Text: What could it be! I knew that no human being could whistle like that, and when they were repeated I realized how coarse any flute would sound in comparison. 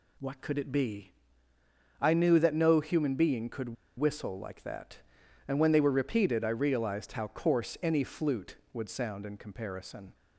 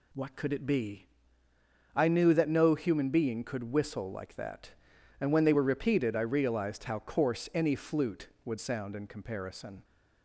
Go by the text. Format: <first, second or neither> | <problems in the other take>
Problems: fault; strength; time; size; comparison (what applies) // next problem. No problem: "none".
second | pauses between "could" and "whistle"; slight; at 3.7 s; 0.24 s long